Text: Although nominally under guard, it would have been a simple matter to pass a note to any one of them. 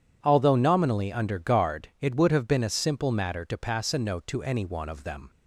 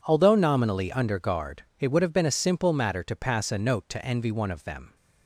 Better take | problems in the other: first | says "envy" for "any"; at 4.0 s

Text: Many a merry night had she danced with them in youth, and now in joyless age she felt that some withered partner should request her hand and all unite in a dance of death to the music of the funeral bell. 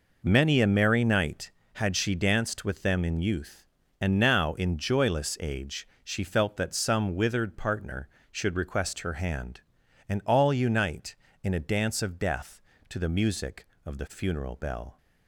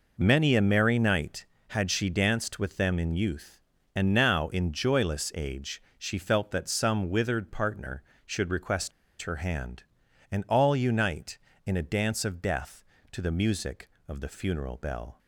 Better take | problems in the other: first | pauses between "age" and "she"; slight; at 5.7 s; 0.16 s long; slight in the first // pauses between "request" and "her"; slight; at 8.9 s; 0.31 s long

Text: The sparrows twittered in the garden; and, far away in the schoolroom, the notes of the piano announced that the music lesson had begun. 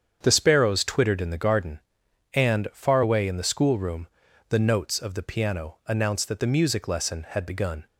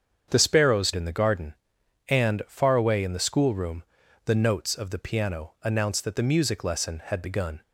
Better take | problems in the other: first | starts louder than the rest; strong; until 1.3 s; 7.5 dB; strong in the first // skips "twittered"; at 0.9 s

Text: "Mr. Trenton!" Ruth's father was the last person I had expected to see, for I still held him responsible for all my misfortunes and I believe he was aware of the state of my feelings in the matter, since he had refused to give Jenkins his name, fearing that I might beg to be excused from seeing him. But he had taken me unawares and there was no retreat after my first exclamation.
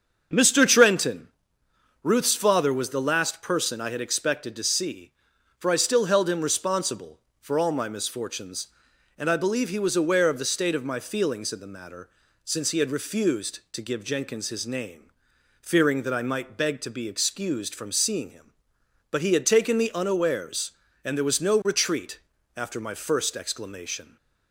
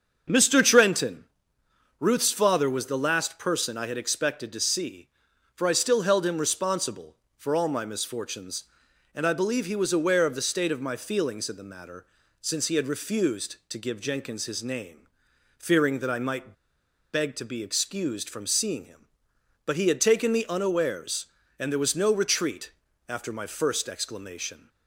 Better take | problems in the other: first | starts louder than the rest; until 2.0 s; 7 dB; also in the first // pauses between "might" and "beg"; noticeable; at 16.5 s; 0.60 s long // pauses between "retreat" and "after"; at 22.7 s; 0.38 s long; also in the first

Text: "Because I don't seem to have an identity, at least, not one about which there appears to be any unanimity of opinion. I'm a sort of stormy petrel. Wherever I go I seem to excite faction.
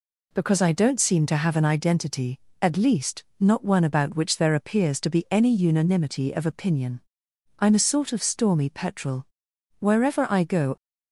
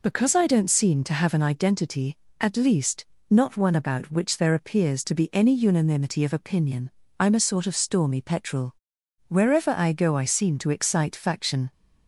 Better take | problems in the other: second | stops before "I seem to excite faction"; at 10.7 s

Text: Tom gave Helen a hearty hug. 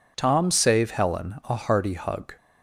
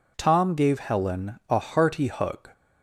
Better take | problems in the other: second | says "save" for "gave"; at 0.5 s

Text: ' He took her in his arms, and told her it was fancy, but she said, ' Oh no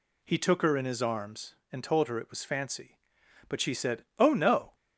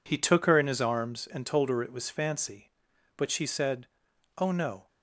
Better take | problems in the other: first | gets quieter; strong; throughout; 18.5 dB

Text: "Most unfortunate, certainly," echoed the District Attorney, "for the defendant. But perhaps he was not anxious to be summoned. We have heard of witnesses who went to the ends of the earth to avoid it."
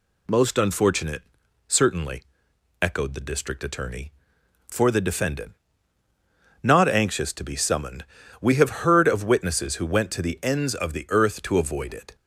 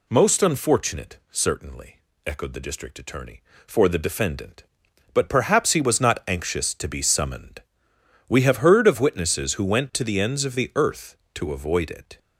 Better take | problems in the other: second | skips "But perhaps he was"; at 6.0 s

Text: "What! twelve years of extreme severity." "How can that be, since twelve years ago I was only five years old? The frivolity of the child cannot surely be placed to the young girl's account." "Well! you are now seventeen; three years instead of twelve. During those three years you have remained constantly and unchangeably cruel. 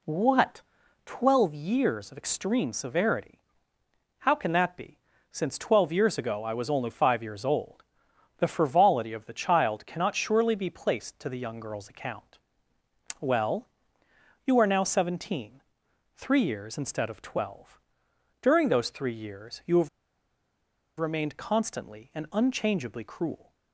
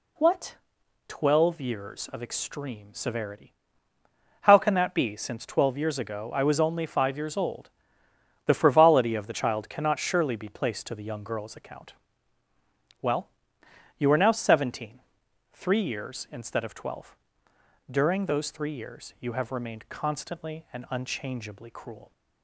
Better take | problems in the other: second | pauses between "have" and "remained"; at 19.8 s; 1.0 s long

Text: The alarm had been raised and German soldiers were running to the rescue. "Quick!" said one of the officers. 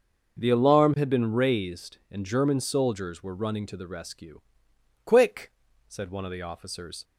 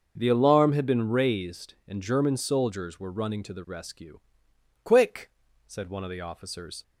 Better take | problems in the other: neither | starts louder than the rest; noticeable; the same in both

